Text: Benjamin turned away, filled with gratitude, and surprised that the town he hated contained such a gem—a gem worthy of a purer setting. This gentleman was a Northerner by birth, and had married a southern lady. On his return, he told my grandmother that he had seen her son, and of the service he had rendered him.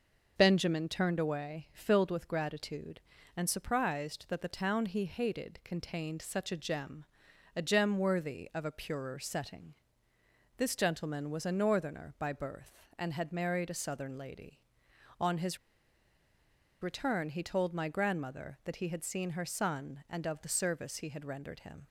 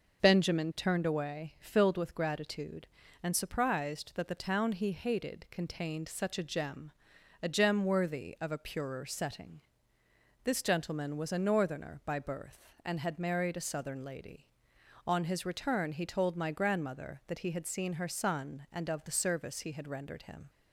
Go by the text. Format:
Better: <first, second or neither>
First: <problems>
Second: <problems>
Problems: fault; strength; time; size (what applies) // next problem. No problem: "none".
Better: second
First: pauses between "his" and "return"; at 15.5 s; 1.2 s long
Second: none